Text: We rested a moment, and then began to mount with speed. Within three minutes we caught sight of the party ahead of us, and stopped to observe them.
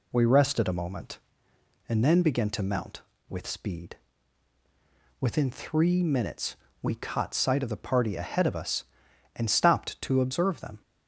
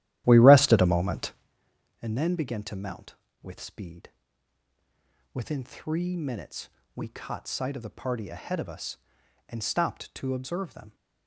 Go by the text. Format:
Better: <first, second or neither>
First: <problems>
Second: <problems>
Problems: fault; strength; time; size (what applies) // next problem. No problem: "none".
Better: first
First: pauses between "minutes" and "we"; slight; at 6.5 s; 0.26 s long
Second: starts louder than the rest; strong; until 1.6 s; 13 dB // pauses between "minutes" and "we"; slight; at 6.7 s; 0.26 s long